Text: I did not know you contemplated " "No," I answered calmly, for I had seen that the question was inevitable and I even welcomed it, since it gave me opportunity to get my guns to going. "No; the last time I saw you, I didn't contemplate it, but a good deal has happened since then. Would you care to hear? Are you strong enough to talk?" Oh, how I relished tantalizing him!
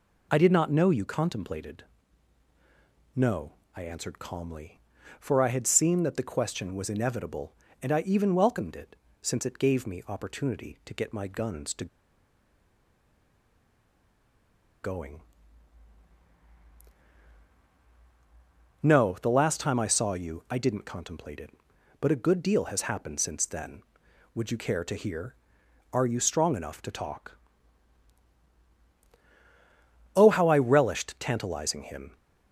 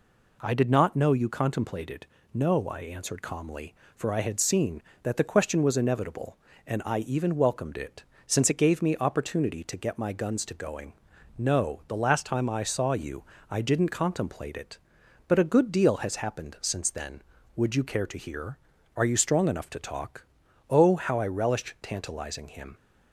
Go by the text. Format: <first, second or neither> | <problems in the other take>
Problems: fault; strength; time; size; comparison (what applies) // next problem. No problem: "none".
second | pauses between "to" and "going"; strong; at 11.8 s; 2.9 s long